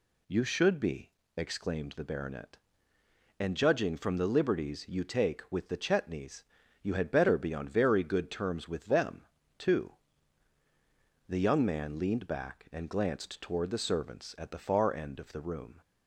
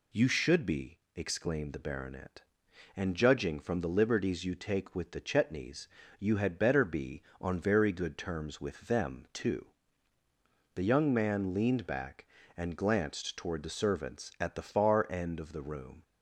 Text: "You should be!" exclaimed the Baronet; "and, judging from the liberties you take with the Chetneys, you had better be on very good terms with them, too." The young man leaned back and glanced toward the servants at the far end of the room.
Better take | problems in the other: neither | none

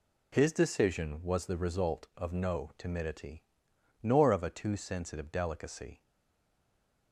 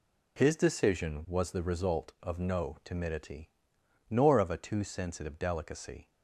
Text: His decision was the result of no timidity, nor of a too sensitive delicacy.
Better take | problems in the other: second | stays silent after the last word; from 6.0 s on; 1.1 s long

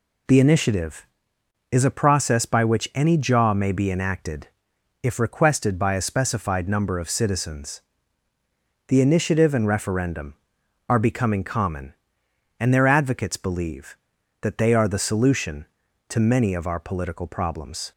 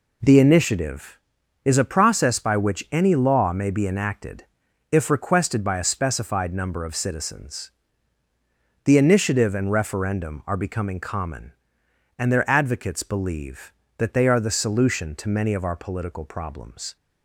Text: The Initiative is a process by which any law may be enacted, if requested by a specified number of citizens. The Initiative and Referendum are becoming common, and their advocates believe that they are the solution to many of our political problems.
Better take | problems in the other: second | says "jaw" for "law"; at 3.1 s

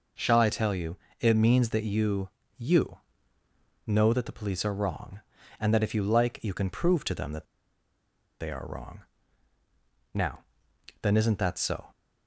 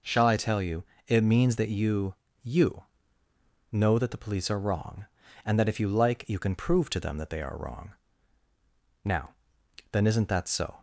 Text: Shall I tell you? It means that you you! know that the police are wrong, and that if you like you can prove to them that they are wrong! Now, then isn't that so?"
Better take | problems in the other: second | pauses between "you" and "you"; slight; at 2.3 s; 0.26 s long; slight in the second // pauses between "that" and "they"; noticeable; at 7.4 s; 0.95 s long

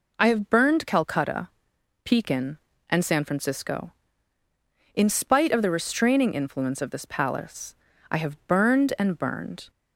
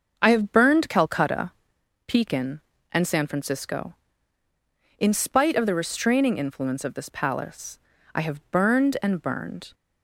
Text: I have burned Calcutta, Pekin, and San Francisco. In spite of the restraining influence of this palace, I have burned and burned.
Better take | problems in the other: first | starts louder than the rest; until 1.9 s; 6.5 dB

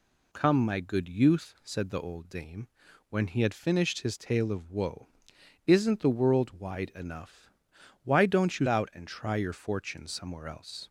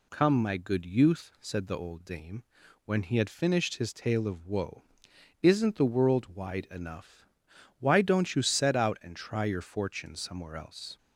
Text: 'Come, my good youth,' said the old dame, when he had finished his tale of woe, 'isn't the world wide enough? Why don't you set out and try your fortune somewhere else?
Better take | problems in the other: second | skips "set"; at 8.6 s

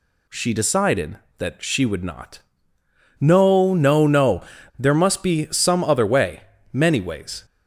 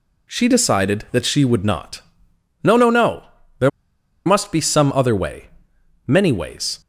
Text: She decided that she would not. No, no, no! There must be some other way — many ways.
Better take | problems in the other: first | pauses between "There" and "must"; noticeable; at 3.6 s; 0.56 s long

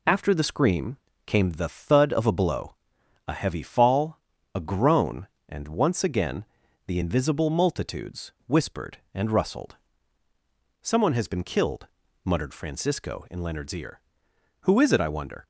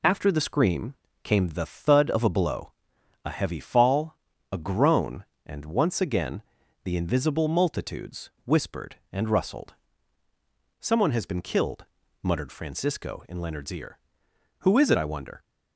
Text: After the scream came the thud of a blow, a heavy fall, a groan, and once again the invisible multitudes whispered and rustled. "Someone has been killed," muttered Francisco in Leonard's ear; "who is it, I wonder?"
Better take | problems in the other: neither | pauses between "scream" and "came"; slight; the same in both // pauses between "again" and "the"; the same in both

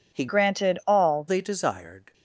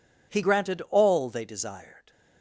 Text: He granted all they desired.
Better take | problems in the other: second | changes voice from "granted" to "all"; from 0.2 to 1.2 s; 1.0 s long

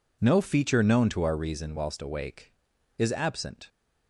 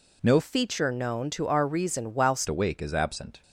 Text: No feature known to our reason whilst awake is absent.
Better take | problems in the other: first | changes voice from "feature" to "whilst"; from 0.3 to 2.4 s; 2.1 s long

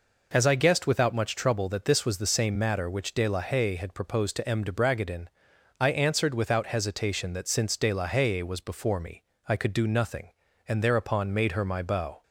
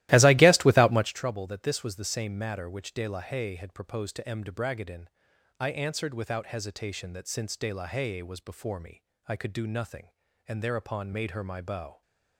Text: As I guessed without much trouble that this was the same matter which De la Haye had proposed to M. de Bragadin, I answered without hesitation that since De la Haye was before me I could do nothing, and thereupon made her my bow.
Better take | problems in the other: first | starts louder than the rest; strong; until 1.2 s; 16 dB // pauses between "me" and "I"; slight; at 9.0 s; 0.24 s long; slight in the first

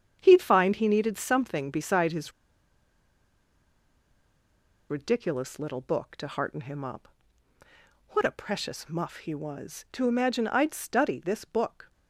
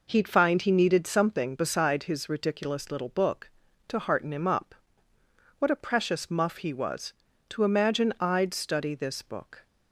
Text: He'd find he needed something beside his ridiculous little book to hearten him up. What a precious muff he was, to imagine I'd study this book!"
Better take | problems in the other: second | starts louder than the rest; strong; until 1.2 s; 8 dB // pauses between "his" and "ridiculous"; strong; at 2.3 s; 2.5 s long

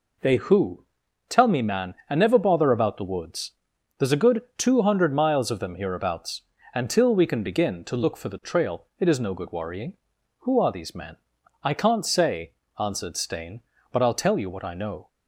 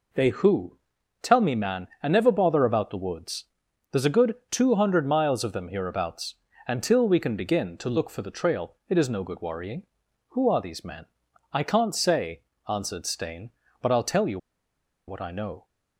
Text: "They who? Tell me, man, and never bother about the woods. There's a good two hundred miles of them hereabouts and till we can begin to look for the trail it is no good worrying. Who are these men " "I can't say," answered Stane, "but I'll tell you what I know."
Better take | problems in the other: first | pauses between "you" and "what"; noticeable; at 14.3 s; 0.70 s long

